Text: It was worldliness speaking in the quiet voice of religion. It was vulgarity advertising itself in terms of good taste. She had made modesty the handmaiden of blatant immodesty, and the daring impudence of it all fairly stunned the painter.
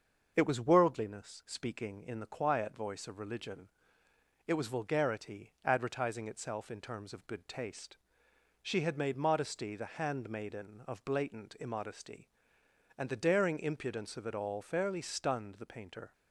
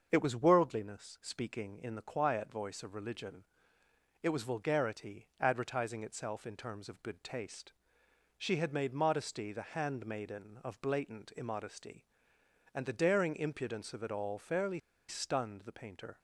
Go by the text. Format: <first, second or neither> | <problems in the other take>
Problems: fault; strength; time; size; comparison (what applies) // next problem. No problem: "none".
first | starts louder than the rest; until 1.1 s; 6.5 dB; also in the first // pauses between "fairly" and "stunned"; slight; at 14.7 s; 0.28 s long